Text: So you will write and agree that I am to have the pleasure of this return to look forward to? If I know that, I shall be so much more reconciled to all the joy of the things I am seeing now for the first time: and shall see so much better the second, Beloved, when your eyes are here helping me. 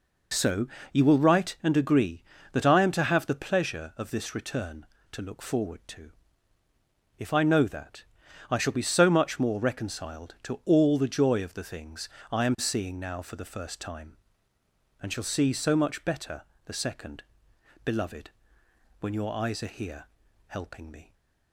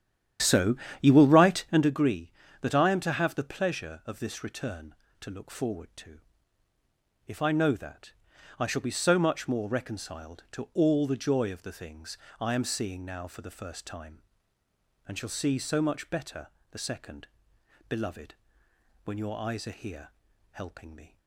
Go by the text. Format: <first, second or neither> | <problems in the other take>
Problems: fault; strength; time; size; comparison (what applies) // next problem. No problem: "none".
first | starts louder than the rest; strong; until 1.9 s; 10 dB // pauses between "So" and "you"; slight; at 0.7 s; 0.26 s long; slight in the first // pauses between "things" and "I"; slight; at 12.1 s; 0.22 s long; slight in the first // pauses between "better" and "the"; slight; at 16.4 s; 0.24 s long; slight in the first // pauses between "here" and "helping"; at 20.1 s; 0.40 s long; also in the first